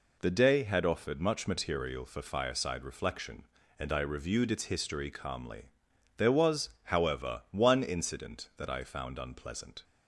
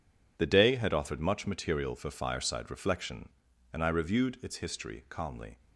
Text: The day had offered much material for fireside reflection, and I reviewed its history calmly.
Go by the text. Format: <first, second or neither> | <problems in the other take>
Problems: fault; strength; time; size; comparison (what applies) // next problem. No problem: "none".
second | goes on to say "There was however one incident that I found unpleasant"; strong; from 6.1 s on; 3.6 s long